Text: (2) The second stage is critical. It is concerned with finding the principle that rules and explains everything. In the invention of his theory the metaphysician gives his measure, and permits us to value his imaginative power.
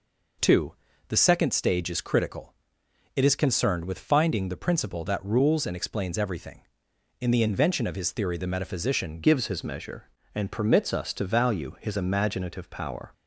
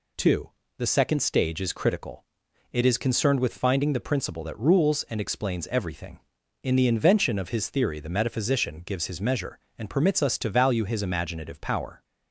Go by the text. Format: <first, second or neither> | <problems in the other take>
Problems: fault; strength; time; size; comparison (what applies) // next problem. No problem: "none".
second | changes voice at "gives"; from 9.2 s on; 3.9 s long